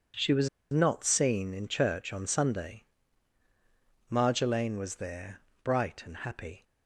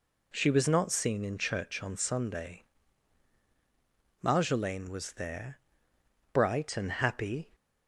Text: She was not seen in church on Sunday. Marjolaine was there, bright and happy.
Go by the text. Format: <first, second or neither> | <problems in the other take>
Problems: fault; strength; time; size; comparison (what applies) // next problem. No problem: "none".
second | pauses between "was" and "not"; slight; at 0.4 s; 0.22 s long